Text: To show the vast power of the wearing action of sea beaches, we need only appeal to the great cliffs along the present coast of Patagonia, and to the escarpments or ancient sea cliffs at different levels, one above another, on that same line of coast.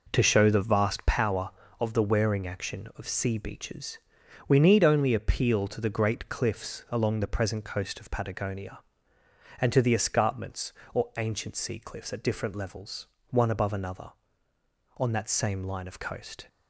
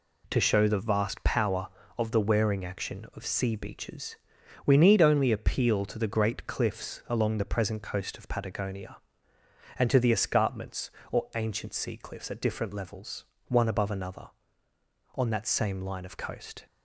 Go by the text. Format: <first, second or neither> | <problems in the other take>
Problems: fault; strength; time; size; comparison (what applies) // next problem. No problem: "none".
second | starts louder than the rest; noticeable; until 1.2 s; 4.5 dB